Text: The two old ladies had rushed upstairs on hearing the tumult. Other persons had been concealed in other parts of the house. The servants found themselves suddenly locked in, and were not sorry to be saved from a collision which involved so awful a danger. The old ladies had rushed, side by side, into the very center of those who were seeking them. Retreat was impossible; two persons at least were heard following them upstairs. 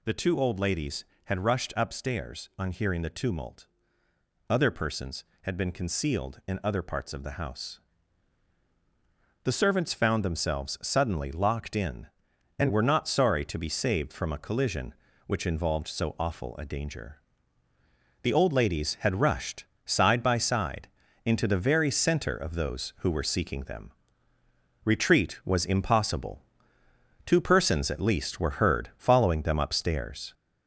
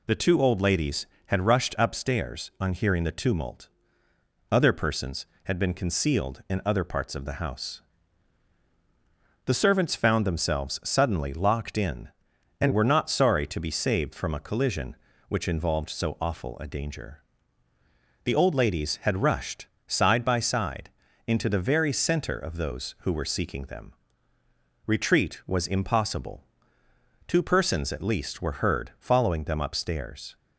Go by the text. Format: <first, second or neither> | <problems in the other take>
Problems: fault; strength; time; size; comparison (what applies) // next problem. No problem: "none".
second | gets louder; noticeable; throughout; 4 dB